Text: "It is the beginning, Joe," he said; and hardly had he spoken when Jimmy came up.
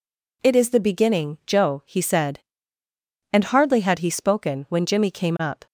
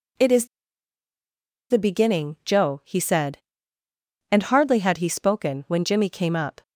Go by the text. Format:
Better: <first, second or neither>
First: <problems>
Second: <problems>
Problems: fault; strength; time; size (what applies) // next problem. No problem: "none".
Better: first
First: none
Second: pauses between "is" and "the"; strong; at 0.4 s; 1.2 s long